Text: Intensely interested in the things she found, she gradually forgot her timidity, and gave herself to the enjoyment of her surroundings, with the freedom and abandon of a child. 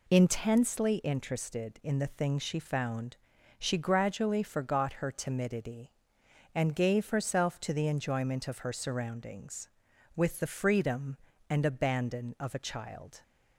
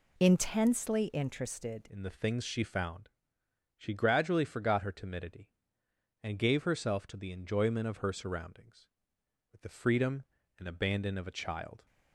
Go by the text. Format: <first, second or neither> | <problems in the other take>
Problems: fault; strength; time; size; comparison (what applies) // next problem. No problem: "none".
first | changes voice at "in"; from 1.8 s on; 10.0 s long